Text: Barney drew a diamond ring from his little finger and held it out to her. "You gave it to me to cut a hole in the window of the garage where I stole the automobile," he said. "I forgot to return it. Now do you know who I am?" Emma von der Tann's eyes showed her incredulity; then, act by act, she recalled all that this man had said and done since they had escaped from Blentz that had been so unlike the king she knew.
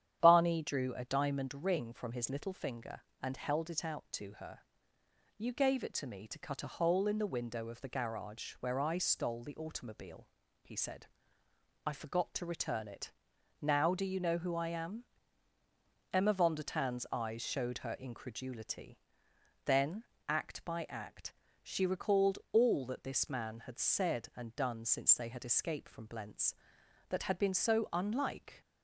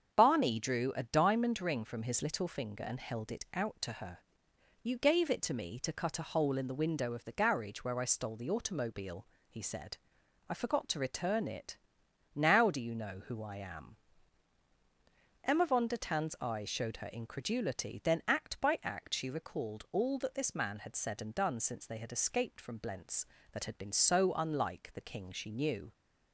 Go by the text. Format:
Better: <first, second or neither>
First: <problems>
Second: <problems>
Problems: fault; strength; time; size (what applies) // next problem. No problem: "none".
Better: second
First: starts louder than the rest; strong; until 1.2 s; 9.5 dB // pauses between "recalled" and "all"; slight; at 22.3 s; 0.15 s long // stops before "the king she knew"; at 28.6 s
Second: starts louder than the rest; until 1.1 s; 7 dB